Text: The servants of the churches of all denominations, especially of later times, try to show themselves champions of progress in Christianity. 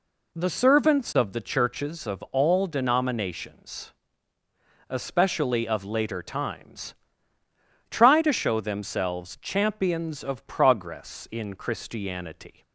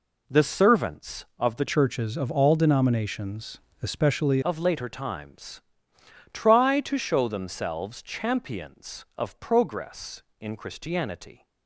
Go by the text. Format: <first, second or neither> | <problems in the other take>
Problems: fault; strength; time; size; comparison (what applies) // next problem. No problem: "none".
first | changes voice from "churches" to "especially"; from 1.6 to 4.4 s; 2.8 s long